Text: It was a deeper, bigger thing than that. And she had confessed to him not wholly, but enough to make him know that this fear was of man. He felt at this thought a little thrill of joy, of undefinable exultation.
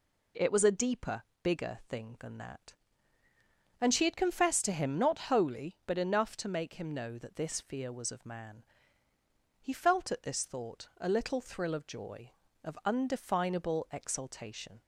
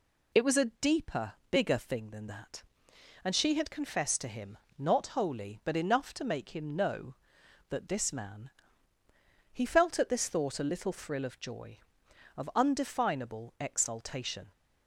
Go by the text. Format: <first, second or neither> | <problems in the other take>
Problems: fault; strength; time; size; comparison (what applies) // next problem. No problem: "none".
first | pauses between "him" and "not"; slight; at 4.5 s; 0.22 s long // skips "fear was of"; at 8.1 s